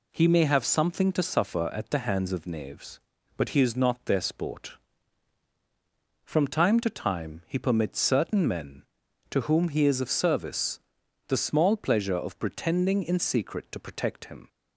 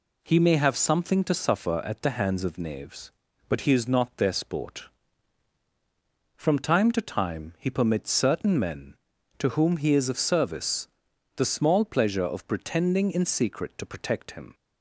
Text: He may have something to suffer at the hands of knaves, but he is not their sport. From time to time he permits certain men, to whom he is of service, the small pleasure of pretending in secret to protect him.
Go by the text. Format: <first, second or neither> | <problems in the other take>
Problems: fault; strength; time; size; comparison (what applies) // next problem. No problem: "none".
neither | none